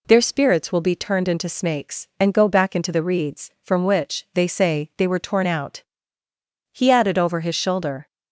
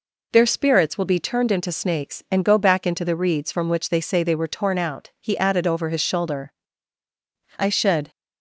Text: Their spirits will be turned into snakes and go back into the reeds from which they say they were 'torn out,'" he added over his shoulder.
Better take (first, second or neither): first